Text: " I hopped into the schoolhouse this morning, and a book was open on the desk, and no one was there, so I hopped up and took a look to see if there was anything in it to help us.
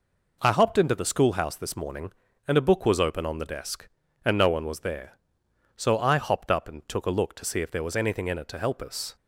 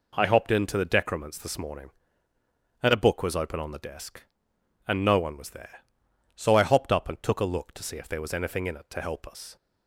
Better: first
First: none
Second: says "decrements" for "schoolhouse"; at 0.8 s

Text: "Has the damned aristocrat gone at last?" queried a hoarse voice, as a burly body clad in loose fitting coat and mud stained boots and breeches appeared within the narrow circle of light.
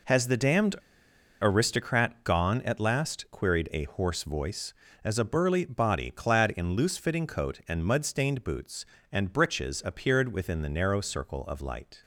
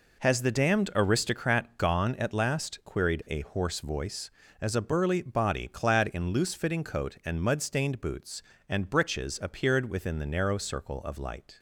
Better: second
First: pauses between "damned" and "aristocrat"; noticeable; at 0.7 s; 0.66 s long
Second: none

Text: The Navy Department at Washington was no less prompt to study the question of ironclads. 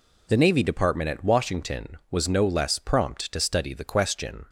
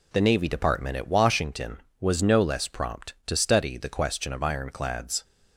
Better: second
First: stops before "of ironclads"; at 4.4 s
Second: none

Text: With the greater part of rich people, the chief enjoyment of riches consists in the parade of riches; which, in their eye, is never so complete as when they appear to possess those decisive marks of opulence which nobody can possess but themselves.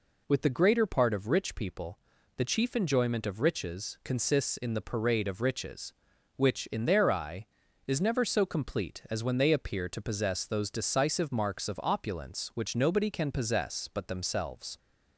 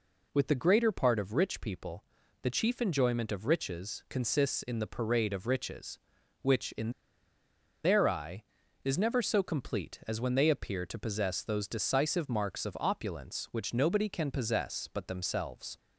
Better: first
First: none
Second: pauses between "in" and "their"; noticeable; at 6.9 s; 0.92 s long

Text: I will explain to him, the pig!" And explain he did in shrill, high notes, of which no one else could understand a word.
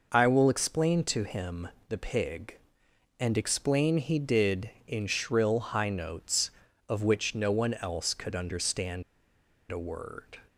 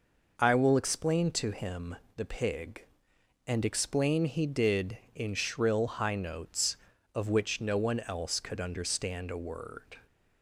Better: second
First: pauses between "understand" and "a"; noticeable; at 9.0 s; 0.67 s long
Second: none

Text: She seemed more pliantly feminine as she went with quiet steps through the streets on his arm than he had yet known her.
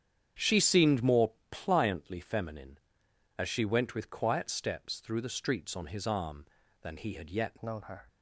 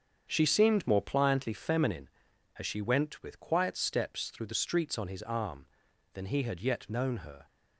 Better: second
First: starts louder than the rest; strong; until 1.5 s; 8.5 dB // pauses between "more" and "pliantly"; slight; at 1.3 s; 0.18 s long // changes voice at "known"; from 7.6 s on; 0.4 s long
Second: starts louder than the rest; strong; until 1.3 s; 7 dB

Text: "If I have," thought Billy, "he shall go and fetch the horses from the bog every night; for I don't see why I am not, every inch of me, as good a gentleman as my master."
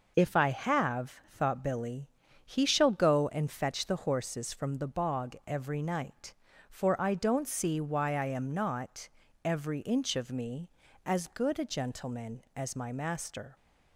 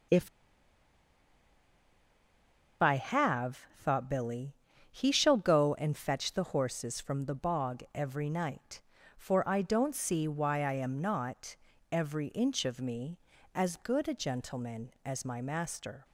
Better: first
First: none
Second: pauses between "If" and "I"; strong; at 0.2 s; 2.5 s long

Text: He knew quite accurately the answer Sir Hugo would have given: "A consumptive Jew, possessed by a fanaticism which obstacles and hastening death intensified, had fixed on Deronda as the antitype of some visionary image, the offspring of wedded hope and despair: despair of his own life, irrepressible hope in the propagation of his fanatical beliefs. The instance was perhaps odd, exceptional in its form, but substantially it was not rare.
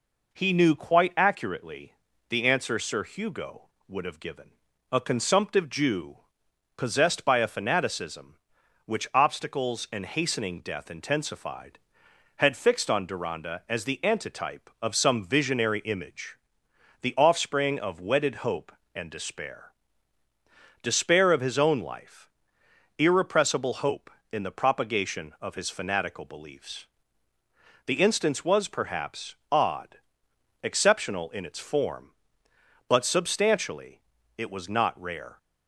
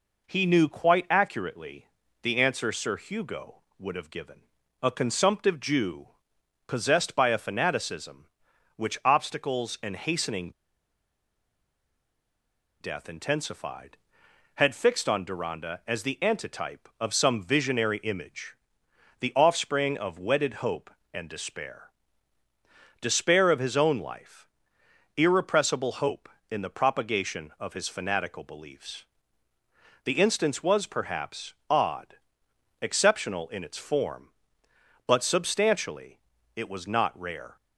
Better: first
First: pauses between "accurately" and "the"; slight; at 1.9 s; 0.34 s long // pauses between "perhaps" and "odd"; slight; at 29.3 s; 0.16 s long // pauses between "substantially" and "it"; slight; at 34.0 s; 0.34 s long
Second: pauses between "accurately" and "the"; slight; at 1.8 s; 0.34 s long // pauses between "hastening" and "death"; strong; at 10.5 s; 2.3 s long // pauses between "perhaps" and "odd"; slight; at 31.5 s; 0.16 s long // pauses between "substantially" and "it"; slight; at 36.1 s; 0.34 s long

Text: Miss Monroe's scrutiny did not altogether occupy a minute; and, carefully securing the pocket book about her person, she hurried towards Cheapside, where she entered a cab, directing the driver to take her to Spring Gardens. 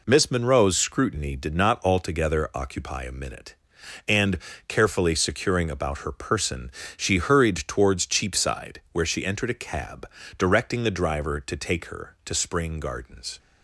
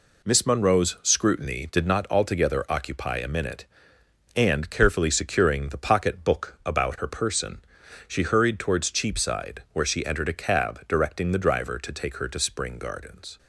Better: second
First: skips "the pocket book"; at 5.7 s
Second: none

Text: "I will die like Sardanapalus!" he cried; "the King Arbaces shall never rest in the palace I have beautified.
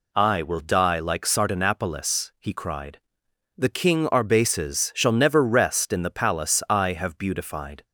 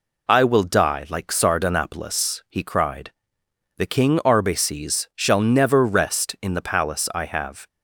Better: first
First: none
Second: stops before "beautified"; at 7.6 s

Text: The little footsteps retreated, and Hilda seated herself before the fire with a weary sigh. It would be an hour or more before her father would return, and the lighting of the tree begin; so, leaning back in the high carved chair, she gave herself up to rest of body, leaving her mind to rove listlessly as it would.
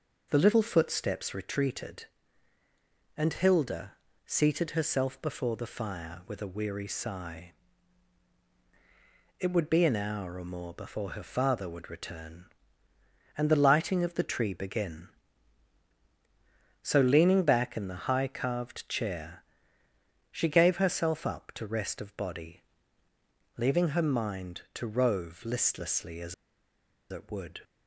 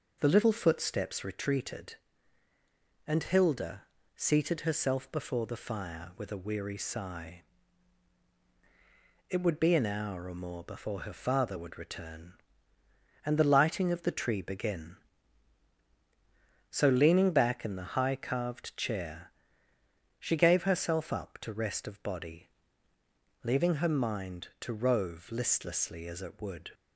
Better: second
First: pauses between "Hilda" and "seated"; slight; at 3.9 s; 0.34 s long // pauses between "as" and "it"; noticeable; at 26.3 s; 0.77 s long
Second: pauses between "Hilda" and "seated"; slight; at 3.8 s; 0.34 s long

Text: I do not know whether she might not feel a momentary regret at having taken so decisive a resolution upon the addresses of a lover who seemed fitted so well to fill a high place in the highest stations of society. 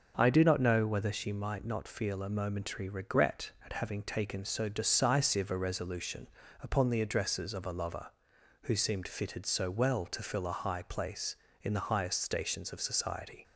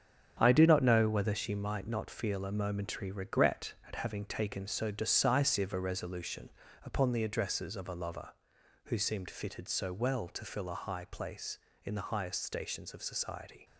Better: first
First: pauses between "resolution" and "upon"; slight; at 6.2 s; 0.36 s long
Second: gets quieter; strong; throughout; 7 dB // pauses between "resolution" and "upon"; slight; at 6.4 s; 0.36 s long

